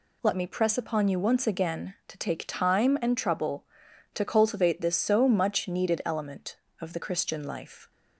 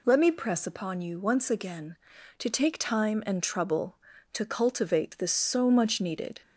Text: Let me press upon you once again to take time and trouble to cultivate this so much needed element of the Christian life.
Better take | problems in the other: first | stops before "element of the Christian life"; at 6.4 s

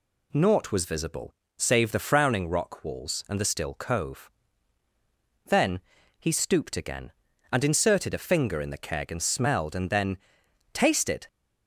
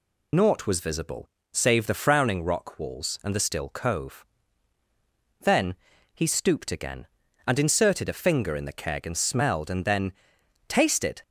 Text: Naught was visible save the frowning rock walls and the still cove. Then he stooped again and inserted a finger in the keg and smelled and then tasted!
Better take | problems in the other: first | loses the start of "Naught"; at 0.3 s; 60 ms // pauses between "visible" and "save"; slight; at 1.2 s; 0.24 s long; slight in the first // pauses between "Then" and "he"; at 5.7 s; 0.38 s long; also in the first // pauses between "then" and "tasted"; noticeable; at 10.1 s; 0.56 s long; noticeable in the first

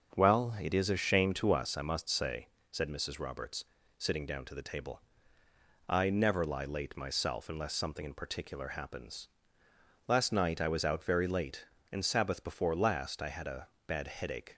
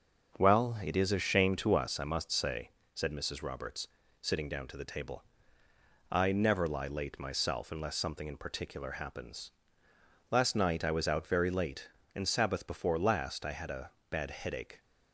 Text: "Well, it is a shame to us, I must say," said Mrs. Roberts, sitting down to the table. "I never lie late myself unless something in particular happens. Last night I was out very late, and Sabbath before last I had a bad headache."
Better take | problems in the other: neither | starts louder than the rest; the same in both // pauses between "a" and "bad"; slight; the same in both

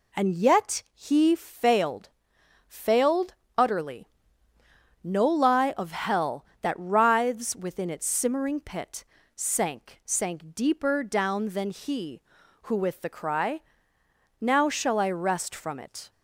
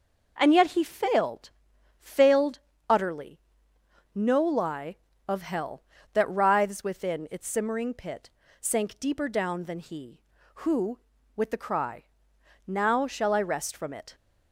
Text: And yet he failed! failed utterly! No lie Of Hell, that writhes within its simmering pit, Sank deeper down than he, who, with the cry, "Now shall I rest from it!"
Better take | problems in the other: second | pauses between "failed" and "utterly"; slight; at 3.3 s; 0.22 s long; slight in the second // says "Sank" twice; at 10.0 s

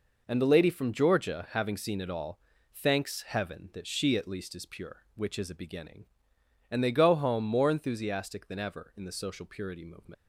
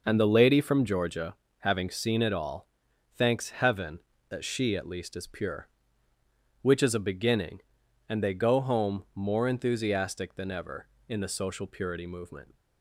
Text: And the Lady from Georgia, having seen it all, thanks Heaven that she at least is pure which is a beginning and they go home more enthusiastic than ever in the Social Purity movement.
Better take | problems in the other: second | leaves "movement" unfinished; at 10.1 s; 95 ms

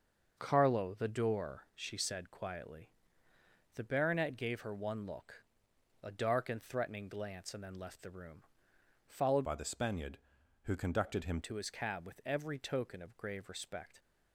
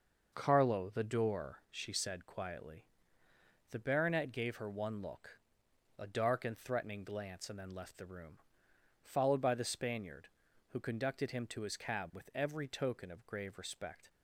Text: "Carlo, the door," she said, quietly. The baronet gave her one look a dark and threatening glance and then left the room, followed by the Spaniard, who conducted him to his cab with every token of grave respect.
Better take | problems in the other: second | starts louder than the rest; noticeable; until 1.3 s; 6 dB // pauses between "look" and "a"; noticeable; at 5.4 s; 0.60 s long; noticeable in the second // changes voice from "by" to "him"; from 9.4 to 11.4 s; 2.0 s long

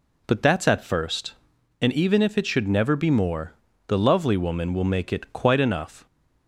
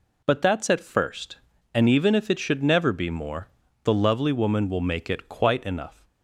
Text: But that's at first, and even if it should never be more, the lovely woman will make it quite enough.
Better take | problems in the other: neither | none

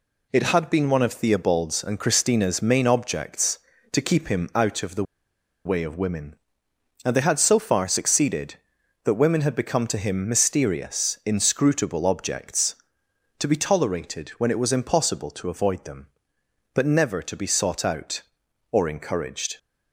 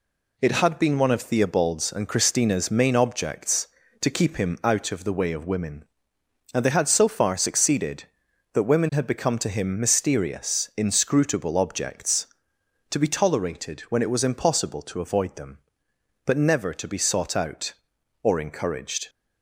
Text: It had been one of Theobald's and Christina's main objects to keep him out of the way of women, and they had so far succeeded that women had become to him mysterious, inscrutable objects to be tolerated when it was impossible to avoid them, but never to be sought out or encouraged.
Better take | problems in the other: second | pauses between "the" and "way"; noticeable; at 5.0 s; 0.61 s long

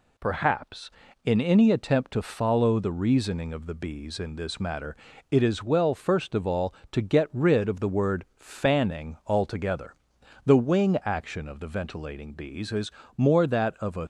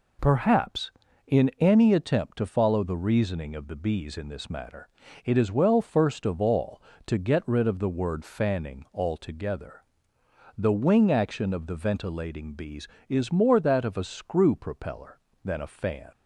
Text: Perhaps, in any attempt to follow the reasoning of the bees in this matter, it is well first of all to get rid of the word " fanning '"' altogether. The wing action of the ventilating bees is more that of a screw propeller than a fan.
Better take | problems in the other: second | pauses between "is" and "more"; slight; at 12.9 s; 0.24 s long // stops before "screw propeller than a fan"; at 14.0 s

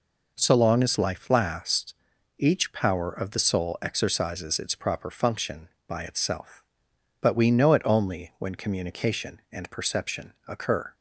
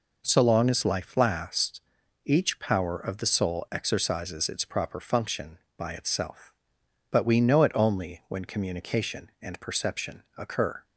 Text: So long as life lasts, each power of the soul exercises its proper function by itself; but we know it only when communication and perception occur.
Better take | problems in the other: neither | pauses between "perception" and "occur"; slight; the same in both

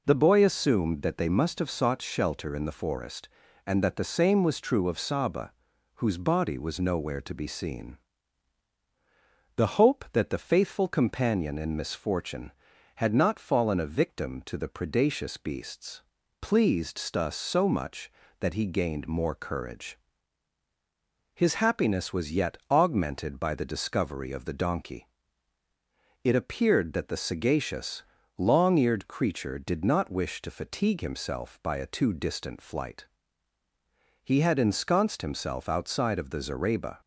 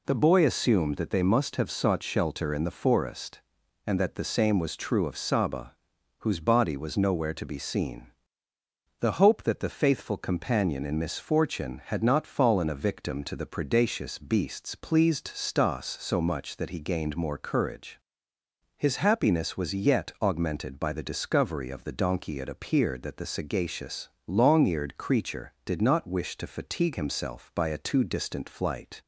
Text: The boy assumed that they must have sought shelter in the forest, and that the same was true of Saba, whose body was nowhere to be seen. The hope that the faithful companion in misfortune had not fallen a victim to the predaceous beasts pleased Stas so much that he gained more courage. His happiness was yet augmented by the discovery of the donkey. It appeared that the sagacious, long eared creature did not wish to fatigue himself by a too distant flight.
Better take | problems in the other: second | pauses between "beasts" and "pleased"; at 16.0 s; 0.40 s long // goes on to say "He had ensconced himself outside of the zareba"; strong; from 34.2 s on; 2.7 s long

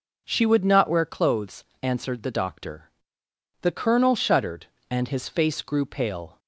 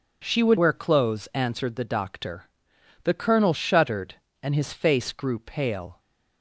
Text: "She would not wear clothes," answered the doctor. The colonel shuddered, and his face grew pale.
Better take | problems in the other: first | skips "not"; at 0.5 s

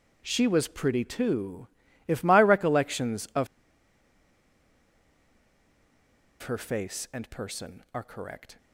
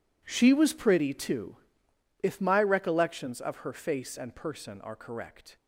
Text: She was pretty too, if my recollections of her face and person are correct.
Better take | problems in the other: second | pauses between "of" and "her"; strong; at 3.4 s; 2.9 s long

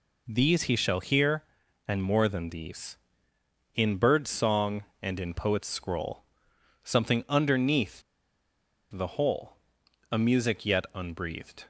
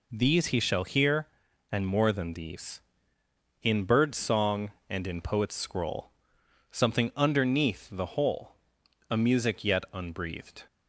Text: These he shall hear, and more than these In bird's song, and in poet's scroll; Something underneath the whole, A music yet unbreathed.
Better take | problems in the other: second | pauses between "underneath" and "the"; noticeable; at 8.0 s; 0.90 s long

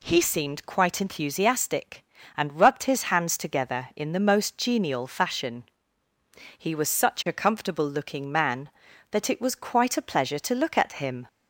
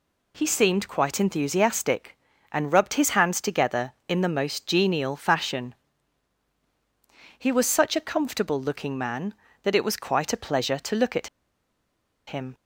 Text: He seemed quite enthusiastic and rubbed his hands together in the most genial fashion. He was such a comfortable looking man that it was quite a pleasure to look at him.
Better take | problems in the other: first | pauses between "at" and "him"; at 11.2 s; 0.99 s long

